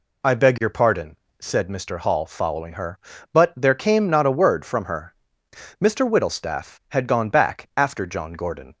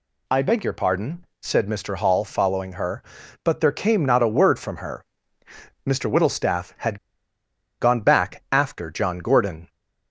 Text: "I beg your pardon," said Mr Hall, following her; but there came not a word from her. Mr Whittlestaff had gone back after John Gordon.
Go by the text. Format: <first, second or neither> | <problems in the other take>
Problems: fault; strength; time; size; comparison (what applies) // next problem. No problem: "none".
first | pauses between "had" and "gone"; noticeable; at 6.9 s; 0.82 s long